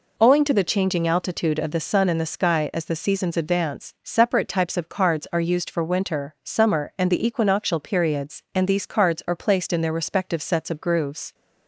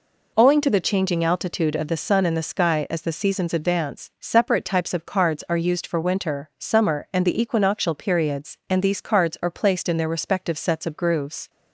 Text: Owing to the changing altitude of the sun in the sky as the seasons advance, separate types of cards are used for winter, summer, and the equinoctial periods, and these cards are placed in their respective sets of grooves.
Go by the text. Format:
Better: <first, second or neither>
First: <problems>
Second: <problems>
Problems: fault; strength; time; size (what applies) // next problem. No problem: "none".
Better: neither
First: none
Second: none